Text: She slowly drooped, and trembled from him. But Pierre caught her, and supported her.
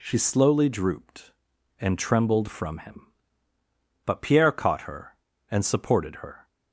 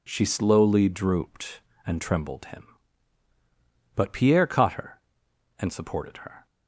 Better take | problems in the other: first | skips "from"; at 2.4 s

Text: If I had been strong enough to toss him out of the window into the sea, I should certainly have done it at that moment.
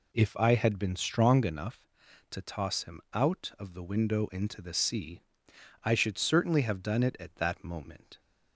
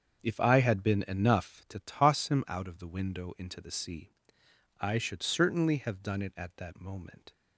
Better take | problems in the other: first | starts louder than the rest; until 1.2 s; 7 dB // skips "strong"; at 1.0 s

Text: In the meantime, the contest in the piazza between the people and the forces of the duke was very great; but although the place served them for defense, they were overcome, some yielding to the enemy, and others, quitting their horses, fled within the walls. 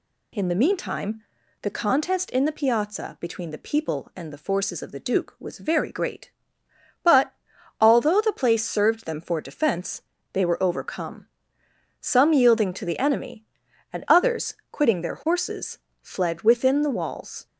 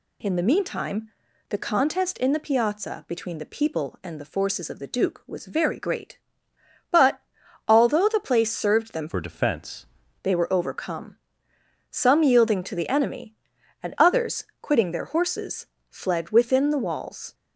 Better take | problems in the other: first | pauses between "but" and "although"; noticeable; at 7.1 s; 0.48 s long; noticeable in the first // changes voice from "for" to "defense"; from 9.0 to 9.8 s; 0.8 s long

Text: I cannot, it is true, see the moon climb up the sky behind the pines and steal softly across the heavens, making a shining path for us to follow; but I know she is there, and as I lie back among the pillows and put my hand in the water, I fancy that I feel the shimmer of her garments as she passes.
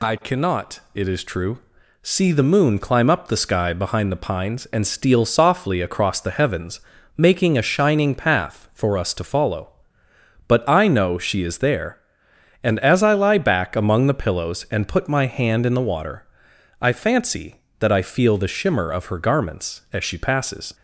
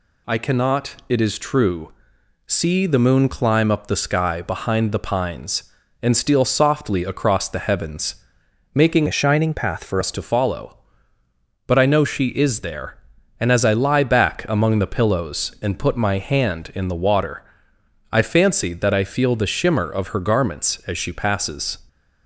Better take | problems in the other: first | changes voice from "a" to "for"; from 9.0 to 10.0 s; 1.0 s long

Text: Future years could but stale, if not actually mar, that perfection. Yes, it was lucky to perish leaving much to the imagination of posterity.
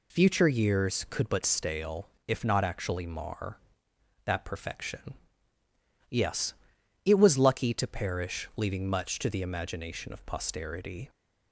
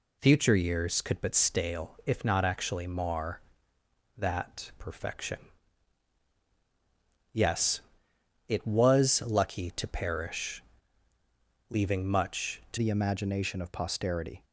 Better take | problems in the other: first | pauses between "perish" and "leaving"; at 10.6 s; 1.1 s long // changes voice at "the"; from 12.7 s on; 1.7 s long

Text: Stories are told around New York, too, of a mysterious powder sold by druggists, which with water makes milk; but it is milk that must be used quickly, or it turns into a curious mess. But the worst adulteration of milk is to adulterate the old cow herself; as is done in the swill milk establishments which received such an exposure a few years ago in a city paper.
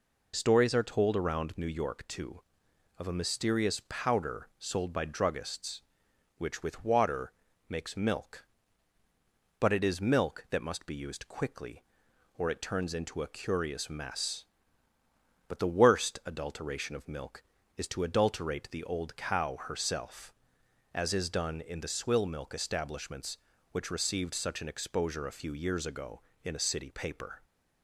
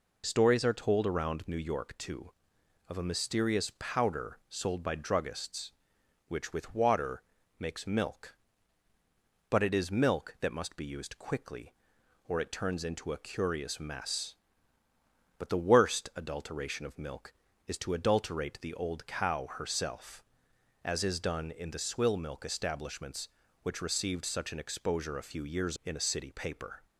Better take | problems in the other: first | pauses between "water" and "makes"; at 7.2 s; 0.38 s long; also in the first // skips "ago"; at 25.7 s

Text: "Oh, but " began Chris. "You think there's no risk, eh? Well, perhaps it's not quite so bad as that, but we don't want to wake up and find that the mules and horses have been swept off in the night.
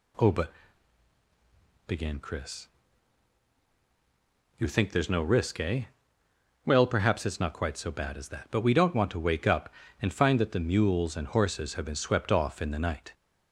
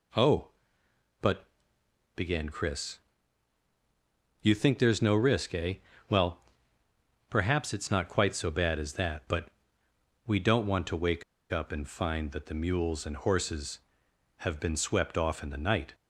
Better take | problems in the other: first | pauses between "but" and "we"; noticeable; at 9.5 s; 0.76 s long // pauses between "wake" and "up"; slight; at 11.2 s; 0.29 s long

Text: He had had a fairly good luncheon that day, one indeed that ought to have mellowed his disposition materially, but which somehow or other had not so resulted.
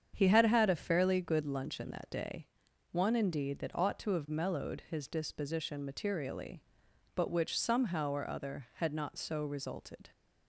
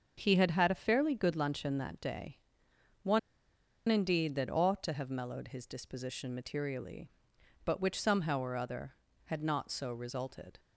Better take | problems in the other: first | starts louder than the rest; until 1.1 s; 6.5 dB; strong in the first // pauses between "one" and "indeed"; noticeable; at 3.1 s; 0.69 s long

